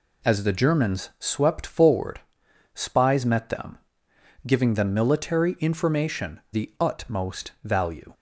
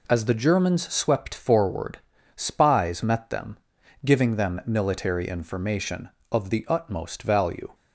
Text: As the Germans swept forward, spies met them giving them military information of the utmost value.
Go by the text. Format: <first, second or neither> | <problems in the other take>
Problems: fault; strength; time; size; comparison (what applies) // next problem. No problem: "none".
second | pauses between "them" and "giving"; noticeable; at 3.7 s; 0.66 s long; noticeable in the second // skips "of"; at 6.4 s